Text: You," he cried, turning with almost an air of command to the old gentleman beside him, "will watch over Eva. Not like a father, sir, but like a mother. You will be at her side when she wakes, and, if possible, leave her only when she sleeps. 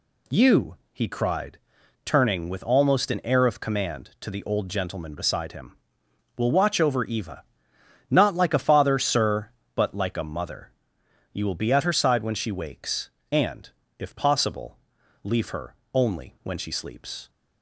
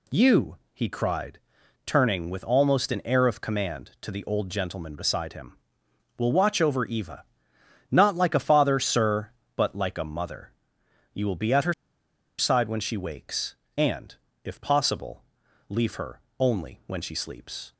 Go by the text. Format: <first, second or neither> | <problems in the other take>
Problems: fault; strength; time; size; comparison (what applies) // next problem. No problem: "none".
first | pauses between "her" and "side"; noticeable; at 11.7 s; 0.64 s long // pauses between "her" and "only"; slight; at 16.2 s; 0.18 s long; slight in the first